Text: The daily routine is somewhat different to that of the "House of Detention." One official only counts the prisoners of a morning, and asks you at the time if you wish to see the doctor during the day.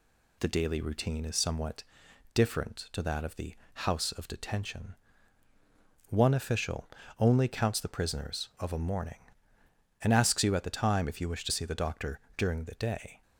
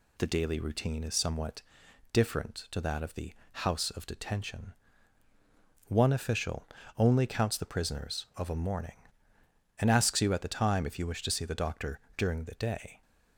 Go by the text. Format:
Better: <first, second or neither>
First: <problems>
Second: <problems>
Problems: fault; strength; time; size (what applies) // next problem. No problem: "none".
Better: neither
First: pauses between "somewhat" and "different"; noticeable; at 1.8 s; 0.52 s long // pauses between "the" and "House"; slight; at 3.5 s; 0.18 s long // pauses between "official" and "only"; slight; at 6.8 s; 0.30 s long // pauses between "doctor" and "during"; slight; at 12.1 s; 0.16 s long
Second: pauses between "somewhat" and "different"; noticeable; at 1.6 s; 0.52 s long // pauses between "the" and "House"; slight; at 3.3 s; 0.18 s long // pauses between "official" and "only"; slight; at 6.6 s; 0.30 s long // pauses between "doctor" and "during"; slight; at 11.9 s; 0.16 s long